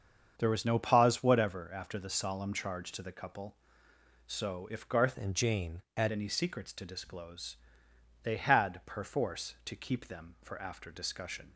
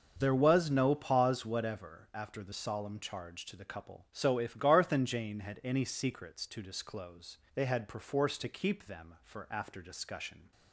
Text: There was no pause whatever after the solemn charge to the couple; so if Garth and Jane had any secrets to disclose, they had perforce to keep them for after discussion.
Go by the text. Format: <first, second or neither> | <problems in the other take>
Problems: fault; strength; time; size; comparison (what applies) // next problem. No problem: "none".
second | starts louder than the rest; until 1.3 s; 7 dB; noticeable in the second // changes voice from "and" to "had"; from 5.1 to 6.1 s; 1.0 s long